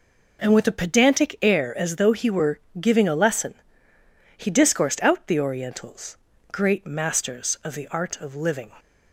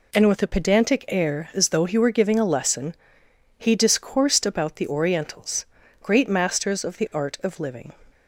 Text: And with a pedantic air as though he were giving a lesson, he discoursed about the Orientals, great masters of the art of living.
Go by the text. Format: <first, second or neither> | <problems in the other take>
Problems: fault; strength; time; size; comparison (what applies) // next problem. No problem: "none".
second | pauses between "were" and "giving"; slight; at 2.5 s; 0.22 s long // says "out" for "about"; at 5.0 s